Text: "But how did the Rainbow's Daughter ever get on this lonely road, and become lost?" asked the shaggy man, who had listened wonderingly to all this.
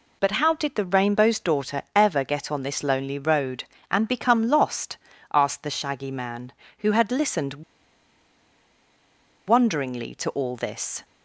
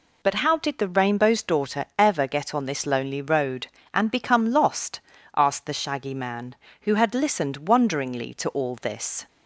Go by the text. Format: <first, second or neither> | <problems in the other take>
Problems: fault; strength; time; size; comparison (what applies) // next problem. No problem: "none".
second | pauses between "listened" and "wonderingly"; strong; at 7.6 s; 1.8 s long